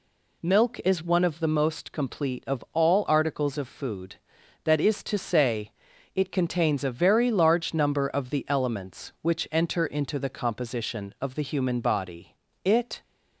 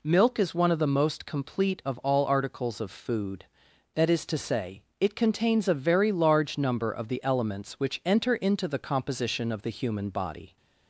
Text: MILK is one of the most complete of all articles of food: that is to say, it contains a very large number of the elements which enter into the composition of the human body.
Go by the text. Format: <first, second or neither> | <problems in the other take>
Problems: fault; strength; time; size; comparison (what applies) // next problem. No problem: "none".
second | goes on to say "It"; slight; from 12.6 s on; 0.38 s long